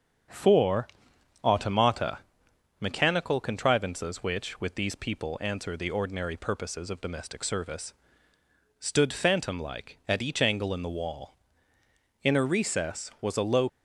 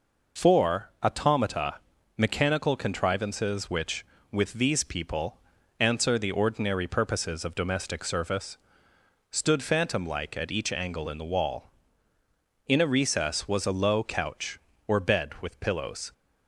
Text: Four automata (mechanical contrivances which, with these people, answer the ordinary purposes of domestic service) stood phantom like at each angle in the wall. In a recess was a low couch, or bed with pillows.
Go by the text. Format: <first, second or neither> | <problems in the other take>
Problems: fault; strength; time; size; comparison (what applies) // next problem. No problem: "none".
second | starts louder than the rest; until 1.8 s; 7 dB // pauses between "Four" and "automata"; noticeable; at 0.8 s; 0.56 s long // stops before "couch or bed with pillows"; at 13.6 s